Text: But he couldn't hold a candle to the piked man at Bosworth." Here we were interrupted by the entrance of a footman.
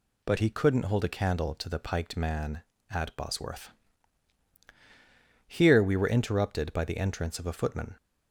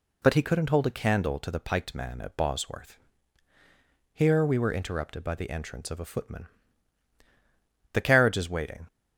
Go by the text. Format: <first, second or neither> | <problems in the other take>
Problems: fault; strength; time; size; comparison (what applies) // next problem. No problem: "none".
first | goes on to say "The carriage is waiting"; noticeable; from 7.8 s on; 1.0 s long